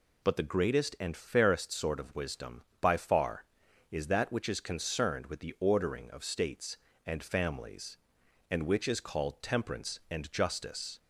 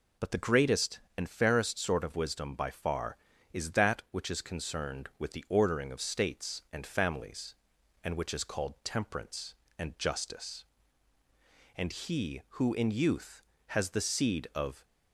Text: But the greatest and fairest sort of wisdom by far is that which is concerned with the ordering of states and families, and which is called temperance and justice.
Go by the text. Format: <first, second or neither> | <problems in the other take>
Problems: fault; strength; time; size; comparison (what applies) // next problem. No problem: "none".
first | goes on to say "And he who in youth has the seed of"; strong; from 11.7 s on; 3.0 s long